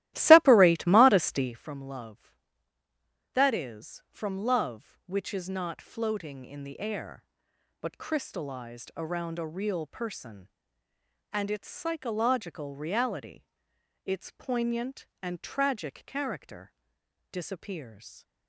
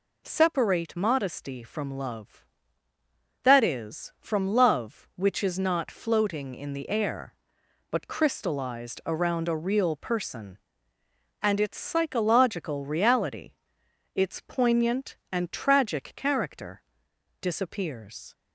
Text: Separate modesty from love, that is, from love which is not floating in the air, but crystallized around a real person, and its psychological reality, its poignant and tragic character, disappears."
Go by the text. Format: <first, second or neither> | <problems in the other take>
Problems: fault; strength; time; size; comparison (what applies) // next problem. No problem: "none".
second | starts louder than the rest; strong; until 1.6 s; 15.5 dB